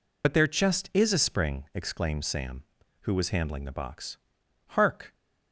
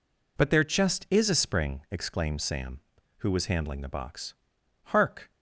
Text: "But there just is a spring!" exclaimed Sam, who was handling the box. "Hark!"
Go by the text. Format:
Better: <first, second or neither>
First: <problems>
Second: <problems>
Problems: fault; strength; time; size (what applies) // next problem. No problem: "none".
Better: second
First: loses the start of "But"; at 0.2 s; 55 ms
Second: none